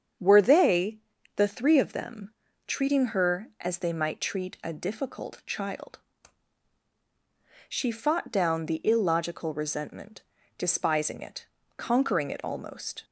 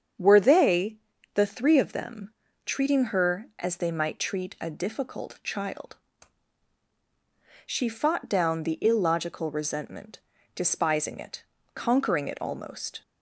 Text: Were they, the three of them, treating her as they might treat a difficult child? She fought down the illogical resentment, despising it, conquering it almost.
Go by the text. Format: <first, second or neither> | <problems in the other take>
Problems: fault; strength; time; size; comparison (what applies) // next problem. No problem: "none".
neither | starts louder than the rest; strong; the same in both